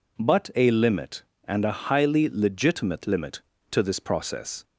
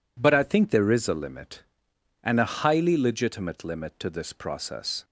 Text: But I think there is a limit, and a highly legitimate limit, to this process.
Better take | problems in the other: second | skips "I think there is"; at 0.5 s

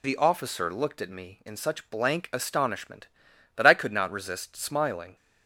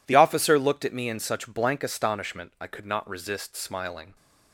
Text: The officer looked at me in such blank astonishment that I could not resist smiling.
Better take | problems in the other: first | skips "that"; at 2.5 s

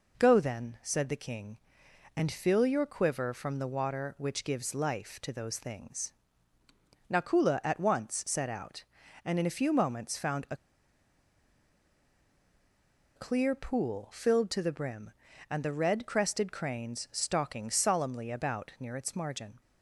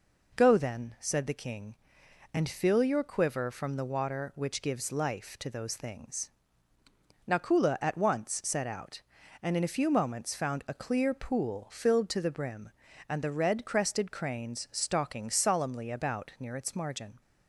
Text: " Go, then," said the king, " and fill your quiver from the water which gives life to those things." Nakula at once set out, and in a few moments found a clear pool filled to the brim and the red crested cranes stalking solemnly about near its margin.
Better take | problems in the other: second | pauses between "a" and "clear"; strong; at 10.5 s; 2.6 s long

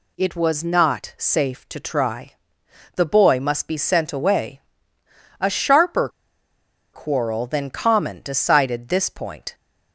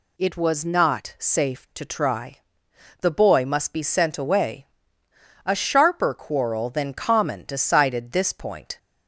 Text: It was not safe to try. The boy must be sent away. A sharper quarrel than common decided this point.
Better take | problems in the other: second | pauses between "sharper" and "quarrel"; noticeable; at 6.0 s; 0.85 s long

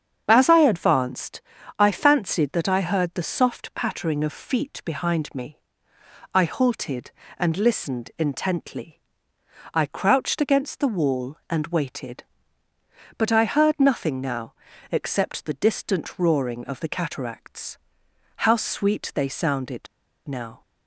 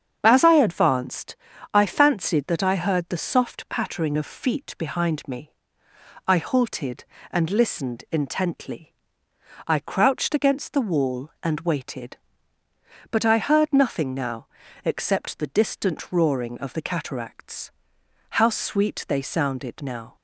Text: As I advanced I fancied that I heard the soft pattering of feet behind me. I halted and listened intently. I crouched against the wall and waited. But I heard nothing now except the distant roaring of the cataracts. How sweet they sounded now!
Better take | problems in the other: second | starts louder than the rest; strong; until 1.2 s; 7.5 dB; strong in the second // pauses between "advanced" and "I"; slight; at 1.4 s; 0.36 s long; slight in the second // pauses between "now" and "except"; slight; at 14.5 s; 0.36 s long; slight in the second // pauses between "sounded" and "now"; at 19.8 s; 0.42 s long

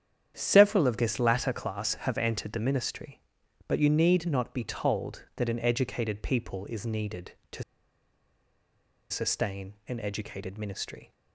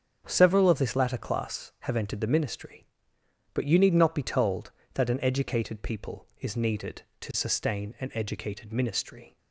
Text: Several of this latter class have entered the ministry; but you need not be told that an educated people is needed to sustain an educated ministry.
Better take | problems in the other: second | starts louder than the rest; strong; until 1.3 s; 9 dB; strong in the second // pauses between "to" and "sustain"; strong; at 7.6 s; 1.4 s long // pauses between "sustain" and "an"; slight; at 9.7 s; 0.16 s long

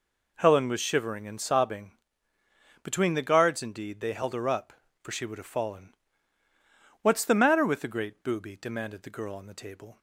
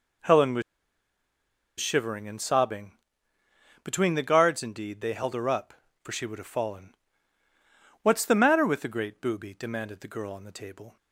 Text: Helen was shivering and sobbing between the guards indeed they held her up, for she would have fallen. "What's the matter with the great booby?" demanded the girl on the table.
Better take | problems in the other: first | pauses between "was" and "shivering"; at 0.6 s; 1.1 s long // pauses between "sobbing" and "between"; noticeable; at 2.9 s; 0.90 s long; noticeable in the first

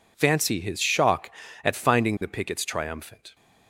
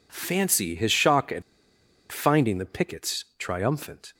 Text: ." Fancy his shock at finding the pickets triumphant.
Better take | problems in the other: first | pauses between "at" and "finding"; noticeable; at 1.4 s; 0.69 s long // pauses between "pickets" and "triumphant"; slight; at 3.2 s; 0.16 s long

